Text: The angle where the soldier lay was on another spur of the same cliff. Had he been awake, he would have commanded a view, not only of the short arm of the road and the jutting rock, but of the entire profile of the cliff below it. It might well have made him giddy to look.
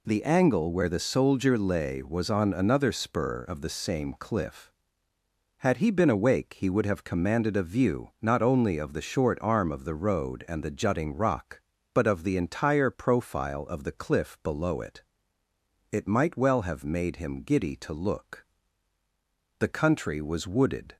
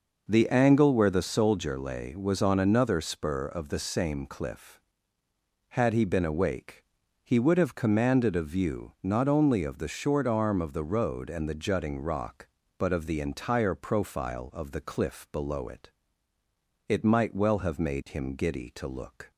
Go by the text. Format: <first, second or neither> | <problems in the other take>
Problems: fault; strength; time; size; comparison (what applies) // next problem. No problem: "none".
second | goes on to say "The country was wooded"; from 19.5 s on; 1.3 s long